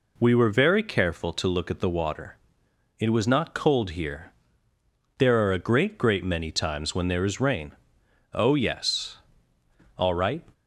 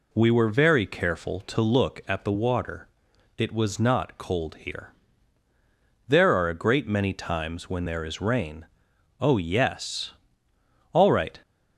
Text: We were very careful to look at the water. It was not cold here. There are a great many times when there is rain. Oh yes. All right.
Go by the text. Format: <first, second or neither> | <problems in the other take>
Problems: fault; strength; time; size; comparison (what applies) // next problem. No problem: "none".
second | says "great" twice; at 5.9 s